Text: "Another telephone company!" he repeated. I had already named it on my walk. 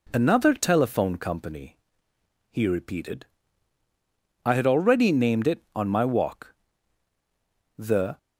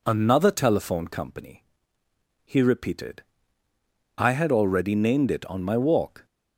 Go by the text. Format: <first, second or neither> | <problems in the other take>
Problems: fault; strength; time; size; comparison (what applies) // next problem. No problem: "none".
second | goes on to say "The"; slight; from 7.7 s on; 0.40 s long